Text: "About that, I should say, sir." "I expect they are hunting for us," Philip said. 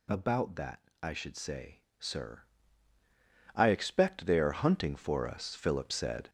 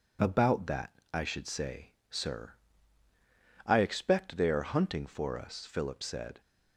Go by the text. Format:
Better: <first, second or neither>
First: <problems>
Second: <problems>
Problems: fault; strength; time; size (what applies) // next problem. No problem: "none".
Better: second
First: gets louder; noticeable; throughout; 6 dB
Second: none